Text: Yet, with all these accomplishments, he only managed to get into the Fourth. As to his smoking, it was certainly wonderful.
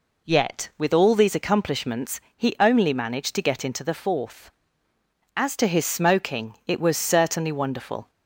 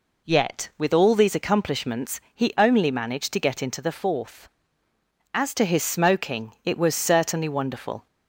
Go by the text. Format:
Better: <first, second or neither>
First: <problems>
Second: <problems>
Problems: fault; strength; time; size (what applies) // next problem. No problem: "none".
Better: neither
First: none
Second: none